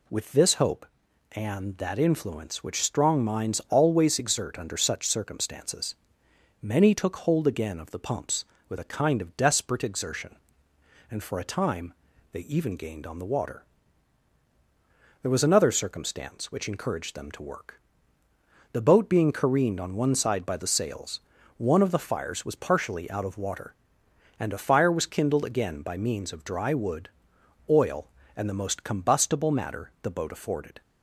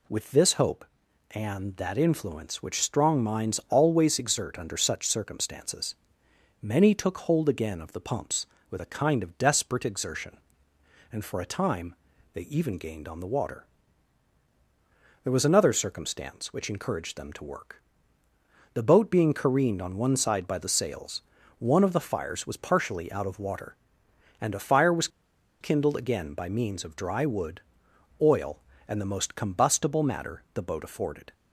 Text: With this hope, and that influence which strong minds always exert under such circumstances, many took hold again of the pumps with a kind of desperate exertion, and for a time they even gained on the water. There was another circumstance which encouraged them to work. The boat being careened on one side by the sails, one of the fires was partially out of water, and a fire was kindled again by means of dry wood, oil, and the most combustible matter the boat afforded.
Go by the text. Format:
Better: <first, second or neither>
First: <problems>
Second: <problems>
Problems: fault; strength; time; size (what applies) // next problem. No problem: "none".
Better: first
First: pauses between "time" and "they"; at 11.9 s; 0.40 s long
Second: pauses between "time" and "they"; at 11.9 s; 0.40 s long // pauses between "was" and "kindled"; noticeable; at 25.0 s; 0.52 s long